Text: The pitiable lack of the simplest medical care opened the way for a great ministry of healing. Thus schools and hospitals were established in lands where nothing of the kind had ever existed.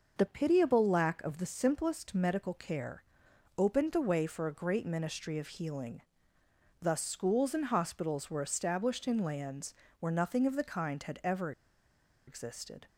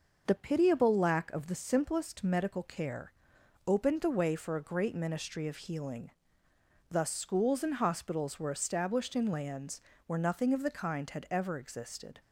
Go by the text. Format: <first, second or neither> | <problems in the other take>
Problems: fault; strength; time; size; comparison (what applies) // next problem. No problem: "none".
second | pauses between "care" and "opened"; noticeable; at 3.0 s; 0.52 s long; noticeable in the second // pauses between "lands" and "where"; slight; at 9.7 s; 0.24 s long; slight in the second // pauses between "ever" and "existed"; noticeable; at 11.5 s; 0.76 s long